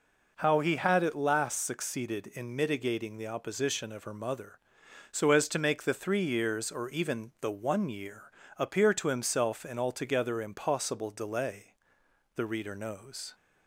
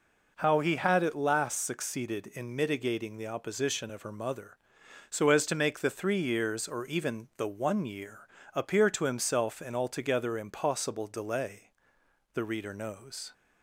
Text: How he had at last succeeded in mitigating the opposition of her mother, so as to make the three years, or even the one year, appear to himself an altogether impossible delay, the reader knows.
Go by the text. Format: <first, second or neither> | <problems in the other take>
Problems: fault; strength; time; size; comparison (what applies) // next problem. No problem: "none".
neither | none